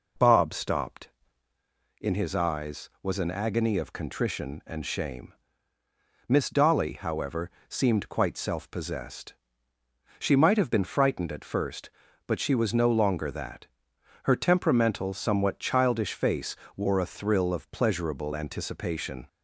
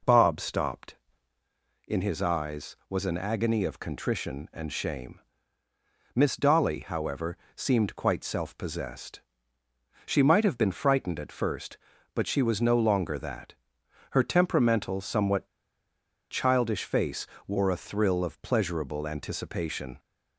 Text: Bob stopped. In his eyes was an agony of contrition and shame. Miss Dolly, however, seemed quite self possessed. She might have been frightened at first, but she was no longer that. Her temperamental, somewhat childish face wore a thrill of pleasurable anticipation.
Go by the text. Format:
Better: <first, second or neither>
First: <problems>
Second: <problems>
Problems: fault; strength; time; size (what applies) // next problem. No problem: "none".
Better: first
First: pauses between "face" and "wore"; slight; at 16.5 s; 0.20 s long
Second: pauses between "somewhat" and "childish"; noticeable; at 15.4 s; 0.84 s long // pauses between "face" and "wore"; slight; at 17.2 s; 0.20 s long